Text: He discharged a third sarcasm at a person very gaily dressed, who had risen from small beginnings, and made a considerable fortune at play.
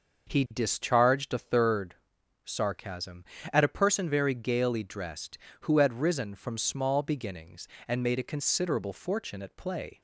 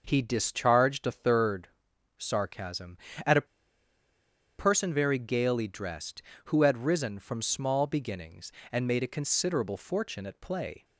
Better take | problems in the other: first | starts louder than the rest; noticeable; until 1.0 s; 6 dB; noticeable in the first // pauses between "third" and "sarcasm"; noticeable; at 1.6 s; 0.52 s long; noticeable in the first // pauses between "a" and "person"; at 3.4 s; 1.1 s long

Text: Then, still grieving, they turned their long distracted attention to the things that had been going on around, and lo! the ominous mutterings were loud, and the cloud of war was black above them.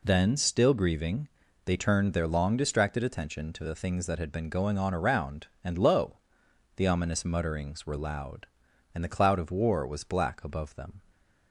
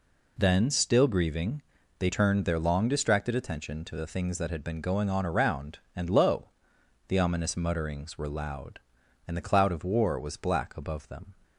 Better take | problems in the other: neither | none

